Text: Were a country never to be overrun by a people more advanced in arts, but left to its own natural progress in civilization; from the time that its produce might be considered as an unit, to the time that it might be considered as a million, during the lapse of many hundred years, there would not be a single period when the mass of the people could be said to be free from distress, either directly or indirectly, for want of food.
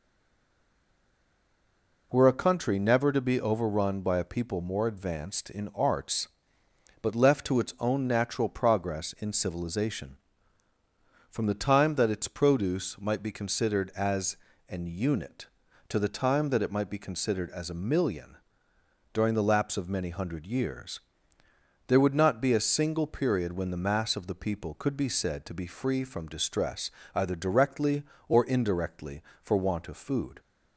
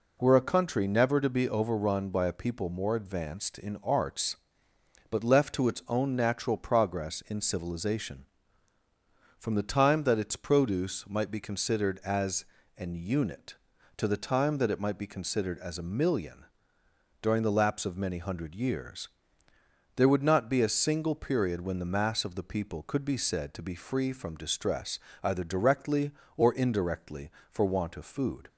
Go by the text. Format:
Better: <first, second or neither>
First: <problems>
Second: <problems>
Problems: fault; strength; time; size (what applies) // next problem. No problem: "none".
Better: second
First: stays silent before the first word; noticeable; until 2.1 s; 2.1 s long // pauses between "as" and "an"; slight; at 14.3 s; 0.30 s long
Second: pauses between "as" and "an"; slight; at 12.4 s; 0.30 s long